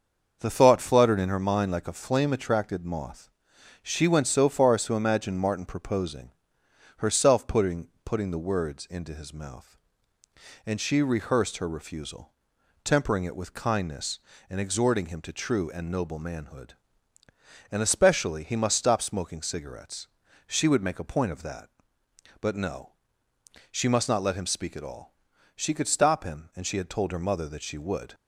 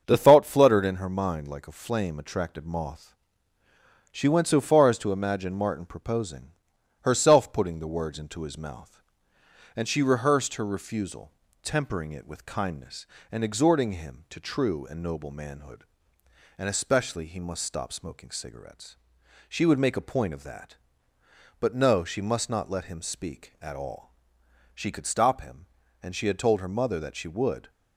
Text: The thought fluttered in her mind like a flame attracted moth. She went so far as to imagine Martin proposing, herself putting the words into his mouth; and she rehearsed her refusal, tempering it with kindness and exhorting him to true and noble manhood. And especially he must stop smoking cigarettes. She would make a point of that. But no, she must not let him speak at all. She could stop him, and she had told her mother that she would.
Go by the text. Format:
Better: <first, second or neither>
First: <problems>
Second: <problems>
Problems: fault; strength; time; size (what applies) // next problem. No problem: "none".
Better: second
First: starts louder than the rest; until 1.4 s; 6.5 dB // says "putting" twice; at 8.0 s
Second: starts louder than the rest; until 1.0 s; 7 dB